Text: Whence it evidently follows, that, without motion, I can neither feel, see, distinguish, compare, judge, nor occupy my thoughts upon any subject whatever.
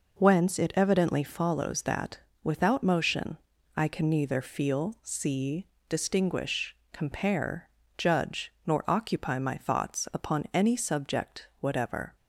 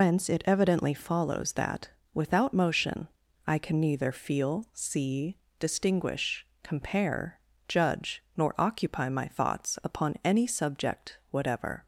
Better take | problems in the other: first | loses the start of "Whence"; at 0.0 s; 125 ms

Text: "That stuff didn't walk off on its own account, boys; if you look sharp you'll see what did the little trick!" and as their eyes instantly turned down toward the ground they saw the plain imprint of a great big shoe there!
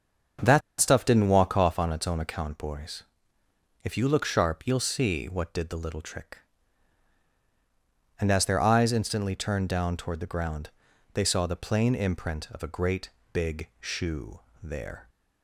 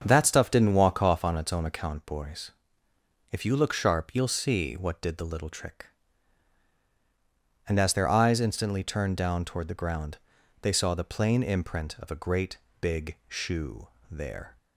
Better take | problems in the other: second | starts louder than the rest; strong; until 1.6 s; 7.5 dB; strong in the second // pauses between "That" and "stuff"; slight; at 0.6 s; 0.19 s long // pauses between "ground" and "they"; at 10.7 s; 0.42 s long; also in the second // pauses between "great" and "big"; slight; at 13.1 s; 0.22 s long; slight in the second // pauses between "shoe" and "there"; slight; at 14.3 s; 0.24 s long; slight in the second

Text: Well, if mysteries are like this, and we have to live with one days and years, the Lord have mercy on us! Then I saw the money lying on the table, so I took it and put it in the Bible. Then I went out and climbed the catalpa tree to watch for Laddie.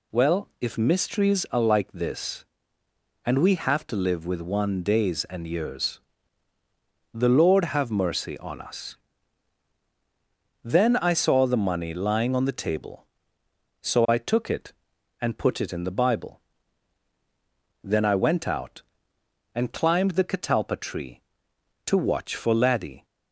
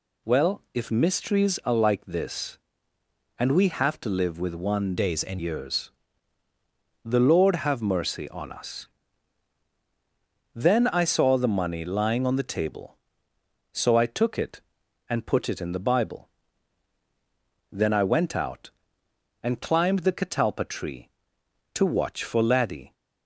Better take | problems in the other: first | changes voice from "days" to "and"; from 4.9 to 5.4 s; 0.5 s long

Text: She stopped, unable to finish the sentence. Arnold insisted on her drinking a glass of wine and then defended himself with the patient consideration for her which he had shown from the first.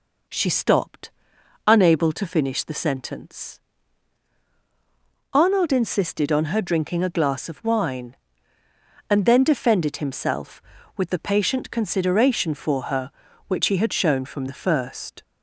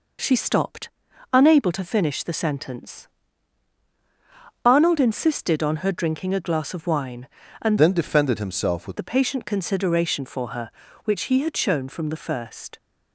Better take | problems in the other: first | changes voice from "then" to "with"; from 7.7 to 8.9 s; 1.2 s long

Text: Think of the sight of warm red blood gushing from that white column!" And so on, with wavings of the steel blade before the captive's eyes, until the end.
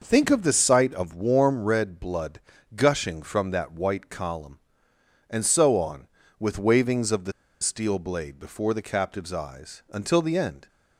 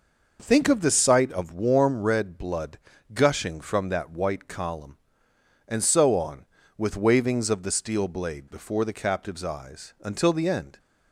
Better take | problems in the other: second | pauses between "blood" and "gushing"; slight; at 2.4 s; 0.34 s long; slight in the second // pauses between "the" and "steel"; slight; at 7.3 s; 0.29 s long

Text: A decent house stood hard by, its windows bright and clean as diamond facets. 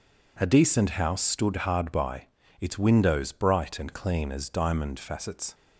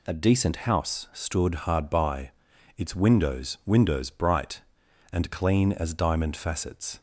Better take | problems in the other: first | says "windows" twice; at 3.6 s

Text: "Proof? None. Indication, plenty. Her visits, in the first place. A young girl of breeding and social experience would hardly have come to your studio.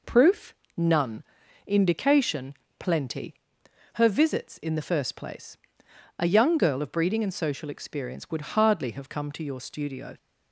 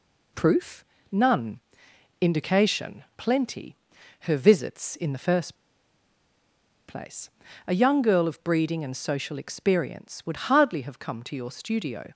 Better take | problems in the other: first | pauses between "first" and "place"; strong; at 5.5 s; 1.3 s long

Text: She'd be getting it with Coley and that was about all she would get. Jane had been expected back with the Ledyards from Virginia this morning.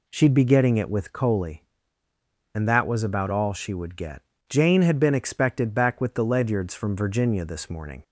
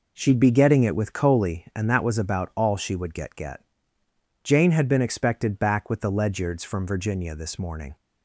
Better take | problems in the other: first | says "get" twice; at 3.3 s

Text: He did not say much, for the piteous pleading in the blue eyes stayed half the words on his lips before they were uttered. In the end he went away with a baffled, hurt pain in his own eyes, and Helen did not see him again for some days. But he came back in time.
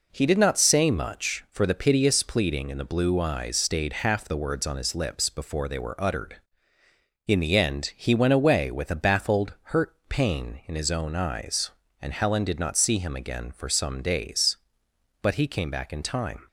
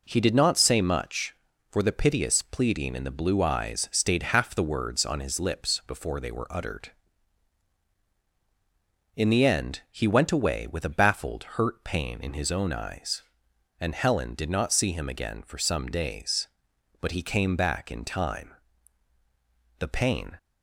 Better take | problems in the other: first | goes on to say "The pain"; from 19.7 s on; 0.58 s long

